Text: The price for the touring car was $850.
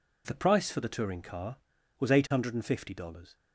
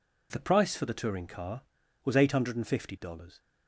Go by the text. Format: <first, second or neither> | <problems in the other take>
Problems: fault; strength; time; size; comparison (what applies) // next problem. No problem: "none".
neither | none